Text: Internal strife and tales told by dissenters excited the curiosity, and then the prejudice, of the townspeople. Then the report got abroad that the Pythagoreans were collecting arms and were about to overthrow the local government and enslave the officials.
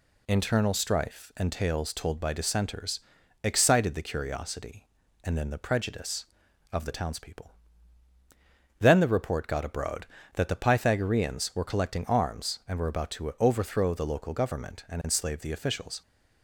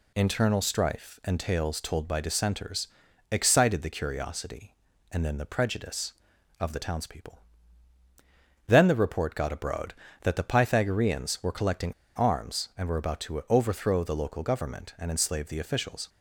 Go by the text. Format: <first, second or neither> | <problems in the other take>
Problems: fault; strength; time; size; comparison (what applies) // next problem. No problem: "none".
first | pauses between "dissenters" and "excited"; at 2.8 s; 0.42 s long; also in the first // pauses between "collecting" and "arms"; slight; at 11.9 s; 0.23 s long